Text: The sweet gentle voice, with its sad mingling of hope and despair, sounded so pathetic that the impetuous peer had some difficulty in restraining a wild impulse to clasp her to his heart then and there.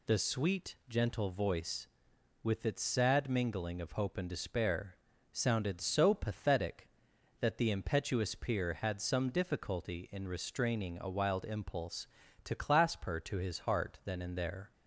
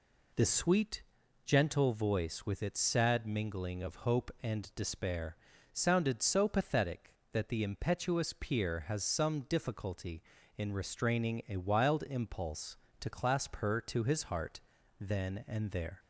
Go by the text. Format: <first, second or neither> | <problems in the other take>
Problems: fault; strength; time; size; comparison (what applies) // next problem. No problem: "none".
first | pauses between "sweet" and "gentle"; at 1.0 s; 0.42 s long // says "has" for "had"; at 8.8 s // pauses between "heart" and "then"; at 14.5 s; 0.40 s long